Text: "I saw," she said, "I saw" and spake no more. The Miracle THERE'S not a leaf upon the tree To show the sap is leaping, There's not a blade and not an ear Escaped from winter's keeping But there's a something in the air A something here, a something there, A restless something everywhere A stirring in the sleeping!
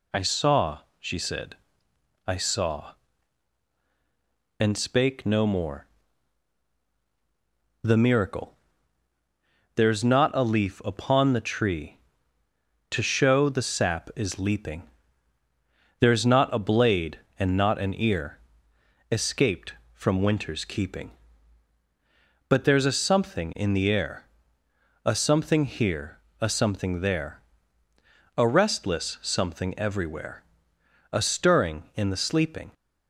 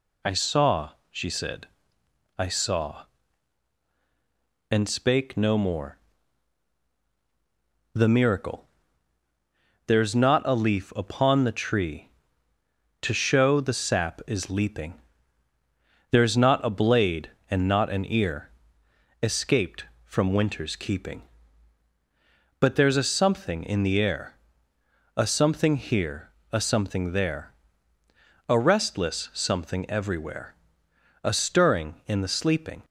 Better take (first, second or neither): neither